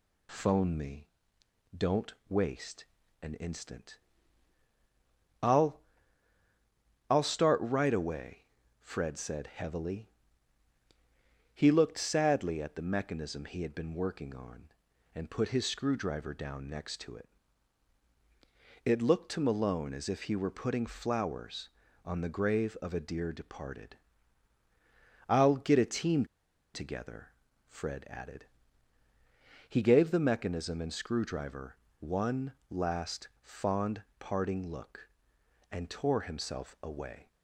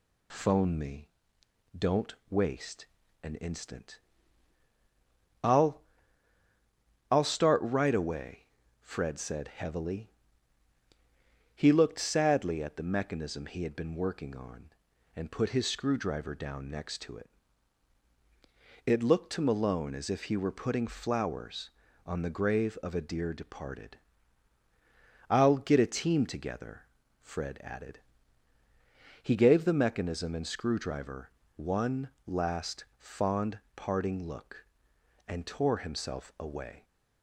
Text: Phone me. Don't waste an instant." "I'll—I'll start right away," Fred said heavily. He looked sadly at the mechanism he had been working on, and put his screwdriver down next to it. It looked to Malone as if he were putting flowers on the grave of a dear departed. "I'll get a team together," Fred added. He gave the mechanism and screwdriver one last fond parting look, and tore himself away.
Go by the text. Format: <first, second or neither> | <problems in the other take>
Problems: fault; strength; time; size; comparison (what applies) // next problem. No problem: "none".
second | pauses between "Don't" and "waste"; slight; at 2.1 s; 0.16 s long; slight in the second // pauses between "waste" and "an"; slight; at 2.8 s; 0.34 s long; slight in the second // pauses between "team" and "together"; noticeable; at 26.2 s; 0.50 s long // pauses between "screwdriver" and "one"; slight; at 31.7 s; 0.24 s long; slight in the second // pauses between "one" and "last"; slight; at 32.5 s; 0.16 s long; slight in the second // pauses between "fond" and "parting"; slight; at 34.0 s; 0.16 s long; slight in the second